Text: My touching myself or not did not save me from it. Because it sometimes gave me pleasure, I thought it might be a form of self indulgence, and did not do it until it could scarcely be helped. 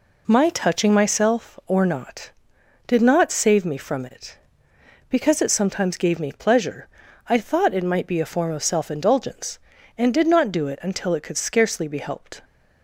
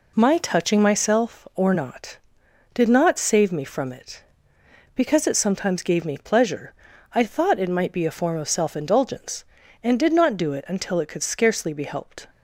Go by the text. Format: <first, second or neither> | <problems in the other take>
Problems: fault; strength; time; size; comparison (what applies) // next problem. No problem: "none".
neither | none